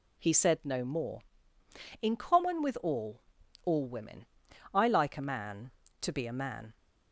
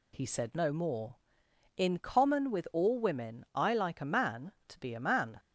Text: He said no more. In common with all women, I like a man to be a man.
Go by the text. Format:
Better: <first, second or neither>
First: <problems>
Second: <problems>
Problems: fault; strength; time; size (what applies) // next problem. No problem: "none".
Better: second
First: says "all" twice; at 3.6 s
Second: none